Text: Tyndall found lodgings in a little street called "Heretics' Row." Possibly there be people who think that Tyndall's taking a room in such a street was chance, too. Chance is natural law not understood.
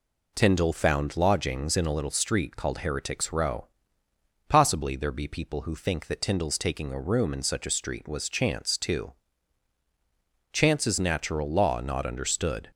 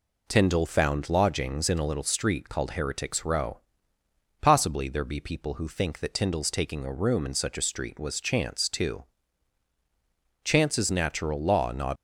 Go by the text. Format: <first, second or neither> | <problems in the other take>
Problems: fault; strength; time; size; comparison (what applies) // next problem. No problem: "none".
first | stops before "understood"; at 11.9 s